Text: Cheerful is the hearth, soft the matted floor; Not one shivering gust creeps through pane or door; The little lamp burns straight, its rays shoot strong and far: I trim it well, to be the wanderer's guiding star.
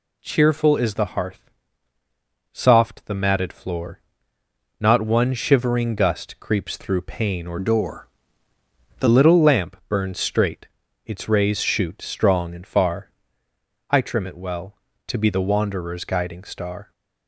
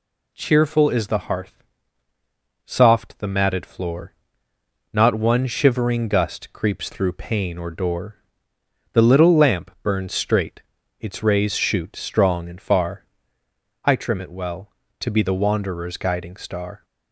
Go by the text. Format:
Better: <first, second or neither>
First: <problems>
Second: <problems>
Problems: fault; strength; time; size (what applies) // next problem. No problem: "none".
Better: second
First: changes voice from "door" to "The"; from 7.5 to 9.0 s; 1.5 s long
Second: none